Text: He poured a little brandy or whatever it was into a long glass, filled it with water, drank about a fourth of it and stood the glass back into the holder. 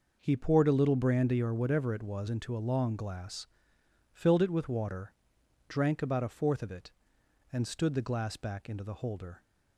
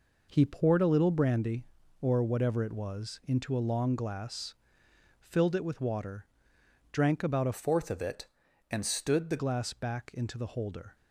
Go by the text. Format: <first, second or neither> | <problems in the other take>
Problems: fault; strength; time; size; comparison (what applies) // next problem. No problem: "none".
first | changes voice from "fourth" to "the"; from 7.5 to 9.3 s; 1.8 s long